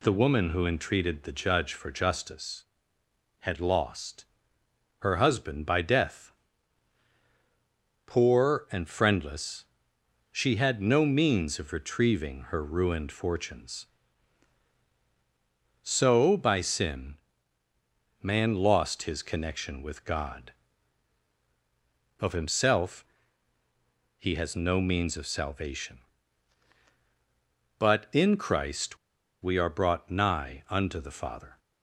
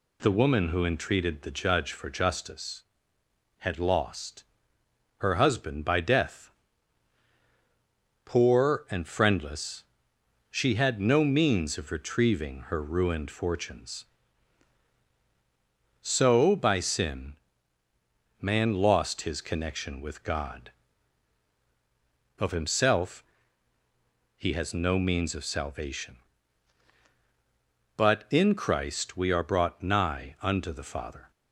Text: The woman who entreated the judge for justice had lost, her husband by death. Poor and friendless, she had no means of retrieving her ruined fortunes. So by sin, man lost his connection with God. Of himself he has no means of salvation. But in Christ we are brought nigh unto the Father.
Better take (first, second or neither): second